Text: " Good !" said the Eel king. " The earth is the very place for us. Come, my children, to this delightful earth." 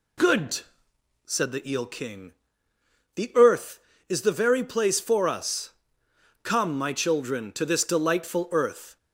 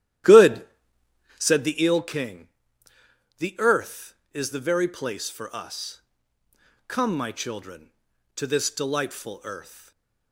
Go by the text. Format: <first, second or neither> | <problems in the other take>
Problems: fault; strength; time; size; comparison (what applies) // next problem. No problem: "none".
first | starts louder than the rest; strong; until 1.7 s; 12 dB // stays silent after the last word; slight; from 9.6 s on; 0.7 s long